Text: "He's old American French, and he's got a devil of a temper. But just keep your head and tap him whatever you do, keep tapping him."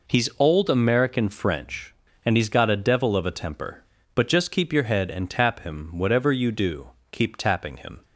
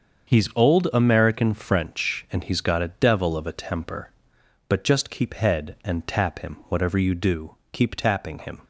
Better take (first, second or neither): first